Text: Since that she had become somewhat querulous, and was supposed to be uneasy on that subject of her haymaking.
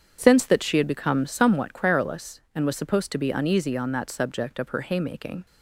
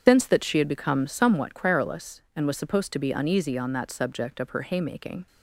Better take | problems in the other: first | loses the start of "Since"; at 0.0 s; 70 ms // starts louder than the rest; strong; until 1.1 s; 8 dB; strong in the first

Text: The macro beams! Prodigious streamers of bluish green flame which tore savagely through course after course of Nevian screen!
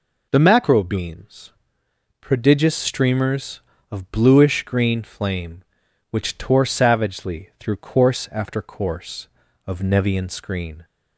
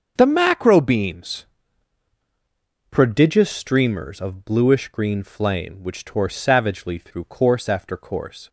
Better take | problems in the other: first | starts louder than the rest; until 1.1 s; 6.5 dB // stops before "of Nevian screen"; at 8.4 s

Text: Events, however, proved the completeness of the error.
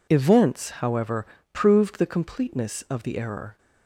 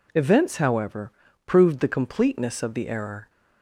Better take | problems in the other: neither | none

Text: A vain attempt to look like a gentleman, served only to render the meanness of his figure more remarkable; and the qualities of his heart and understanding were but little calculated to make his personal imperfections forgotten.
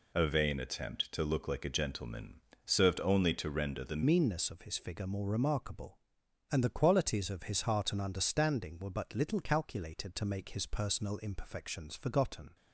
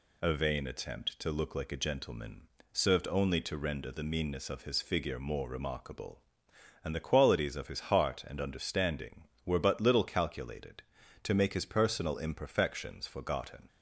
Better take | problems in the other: second | changes voice at "meanness"; from 4.0 s on; 8.5 s long

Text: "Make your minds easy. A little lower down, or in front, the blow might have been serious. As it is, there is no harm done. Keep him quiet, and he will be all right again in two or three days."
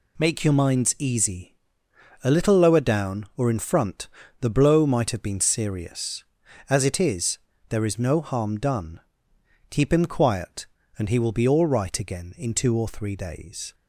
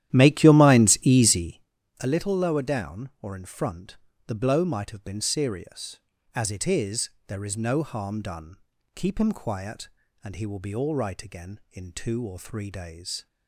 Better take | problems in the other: first | starts louder than the rest; strong; until 1.7 s; 12.5 dB

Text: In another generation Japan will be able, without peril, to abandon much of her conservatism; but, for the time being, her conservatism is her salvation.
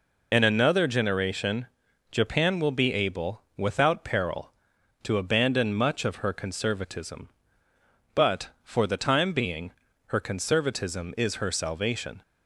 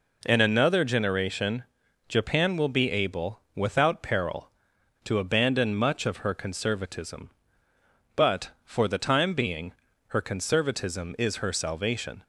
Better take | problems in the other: second | loses the start of "In"; at 0.3 s; 60 ms // pauses between "generation" and "Japan"; at 1.6 s; 0.44 s long; also in the second

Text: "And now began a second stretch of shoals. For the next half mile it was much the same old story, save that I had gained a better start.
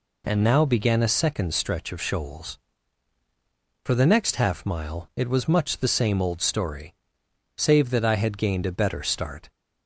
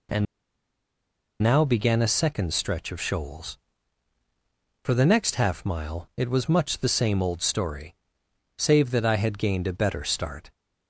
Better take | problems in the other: first | pauses between "And" and "now"; at 0.2 s; 1.1 s long

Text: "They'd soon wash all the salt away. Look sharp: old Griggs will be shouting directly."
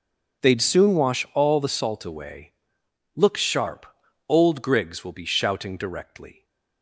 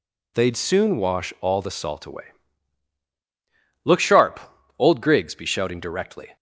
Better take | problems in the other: first | skips "will"; at 5.3 s

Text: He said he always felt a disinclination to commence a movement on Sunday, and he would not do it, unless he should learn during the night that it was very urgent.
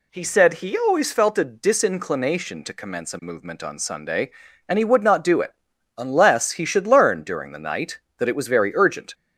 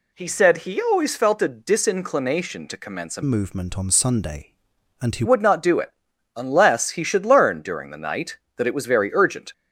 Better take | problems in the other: first | changes voice from "movement" to "he"; from 3.2 to 5.2 s; 2.0 s long

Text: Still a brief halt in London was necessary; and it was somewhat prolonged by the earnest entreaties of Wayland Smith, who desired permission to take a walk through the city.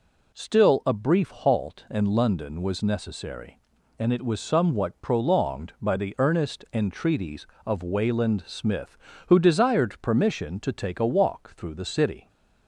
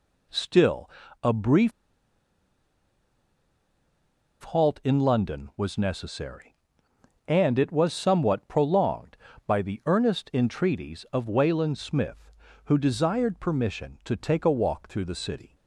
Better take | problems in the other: first | pauses between "Still" and "a"; slight; at 0.8 s; 0.36 s long // pauses between "brief" and "halt"; strong; at 1.7 s; 2.7 s long

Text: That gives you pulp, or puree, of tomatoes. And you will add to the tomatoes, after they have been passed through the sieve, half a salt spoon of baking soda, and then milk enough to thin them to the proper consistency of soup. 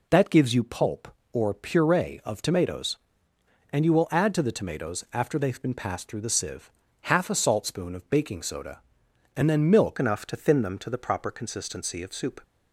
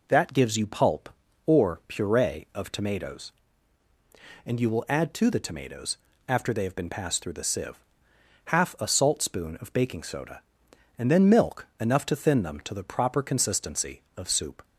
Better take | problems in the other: second | changes voice at "enough"; from 9.9 s on; 2.5 s long

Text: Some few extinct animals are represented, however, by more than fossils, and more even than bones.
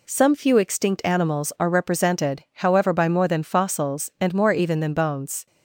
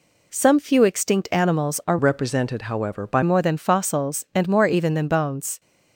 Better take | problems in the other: first | changes voice from "represented" to "by"; from 1.9 to 3.2 s; 1.3 s long

